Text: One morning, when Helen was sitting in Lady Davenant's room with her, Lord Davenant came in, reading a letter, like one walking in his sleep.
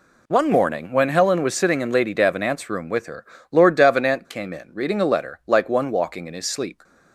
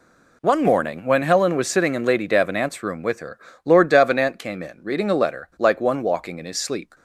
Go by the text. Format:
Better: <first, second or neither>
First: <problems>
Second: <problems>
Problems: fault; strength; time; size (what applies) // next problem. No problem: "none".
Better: neither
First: none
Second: none